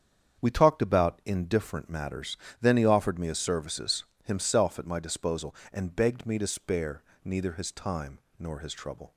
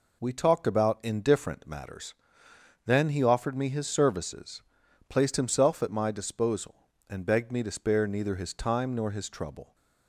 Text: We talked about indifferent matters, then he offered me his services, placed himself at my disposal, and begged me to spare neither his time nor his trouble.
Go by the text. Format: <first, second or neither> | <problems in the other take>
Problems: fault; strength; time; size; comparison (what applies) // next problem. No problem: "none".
second | starts louder than the rest; strong; until 1.4 s; 8 dB // skips "placed"; at 4.1 s // pauses between "spare" and "neither"; slight; at 7.0 s; 0.22 s long // pauses between "time" and "nor"; slight; at 8.1 s; 0.20 s long